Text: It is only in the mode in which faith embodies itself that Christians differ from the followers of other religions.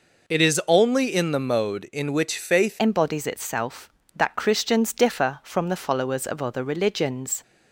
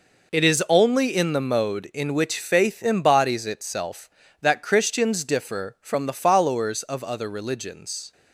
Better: second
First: changes voice at "embodies"; from 2.7 s on; 4.7 s long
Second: none

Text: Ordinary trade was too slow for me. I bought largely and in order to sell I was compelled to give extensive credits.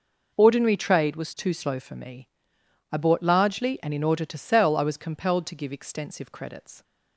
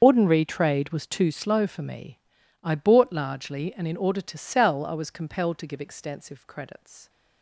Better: first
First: none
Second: loses the start of "Ordinary"; at 0.0 s; 70 ms // starts louder than the rest; until 1.0 s; 7 dB

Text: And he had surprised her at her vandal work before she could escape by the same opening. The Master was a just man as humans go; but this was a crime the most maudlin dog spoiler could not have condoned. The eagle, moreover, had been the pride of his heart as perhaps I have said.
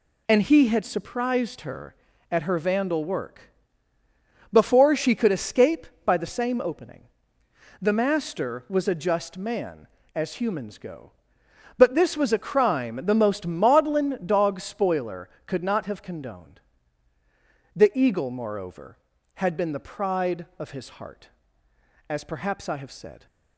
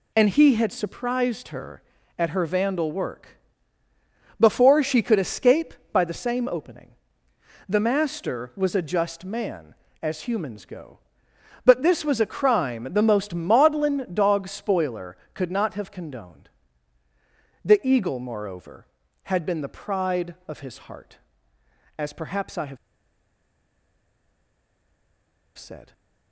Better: first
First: pauses between "work" and "before"; at 3.5 s; 1.0 s long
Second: pauses between "work" and "before"; at 3.3 s; 1.0 s long // pauses between "have" and "said"; strong; at 22.7 s; 2.8 s long

